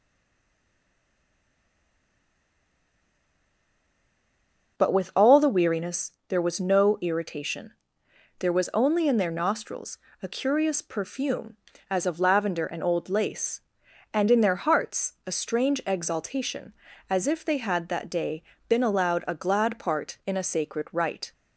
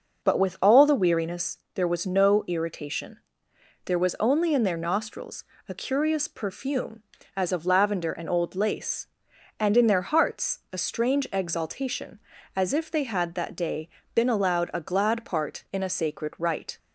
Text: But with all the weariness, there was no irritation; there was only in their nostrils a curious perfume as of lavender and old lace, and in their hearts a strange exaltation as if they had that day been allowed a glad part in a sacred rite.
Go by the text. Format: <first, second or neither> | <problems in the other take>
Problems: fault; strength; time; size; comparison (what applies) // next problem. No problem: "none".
second | stays silent before the first word; strong; until 4.7 s; 4.7 s long // pauses between "nostrils" and "a"; slight; at 9.9 s; 0.26 s long; slight in the second // pauses between "day" and "been"; slight; at 18.4 s; 0.26 s long; slight in the second